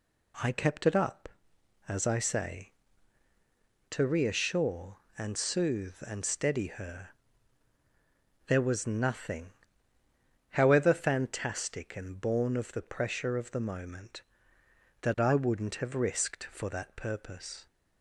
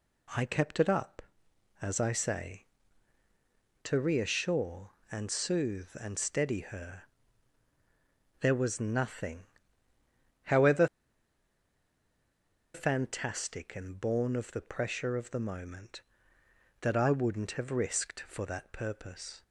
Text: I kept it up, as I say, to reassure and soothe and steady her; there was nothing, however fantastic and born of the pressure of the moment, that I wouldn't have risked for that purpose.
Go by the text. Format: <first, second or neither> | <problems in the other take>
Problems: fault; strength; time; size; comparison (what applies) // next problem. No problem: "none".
first | pauses between "however" and "fantastic"; strong; at 10.8 s; 1.8 s long